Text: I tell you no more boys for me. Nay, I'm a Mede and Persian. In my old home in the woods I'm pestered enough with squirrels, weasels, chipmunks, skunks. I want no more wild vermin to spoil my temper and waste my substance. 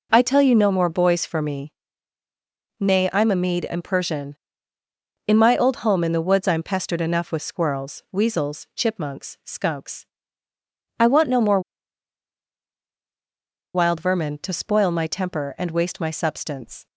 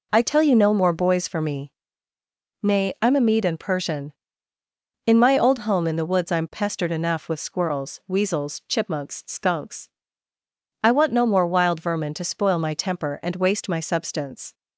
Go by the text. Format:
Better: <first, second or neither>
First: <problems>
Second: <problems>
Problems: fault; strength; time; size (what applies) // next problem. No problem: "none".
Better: second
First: pauses between "more" and "wild"; strong; at 11.6 s; 2.1 s long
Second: none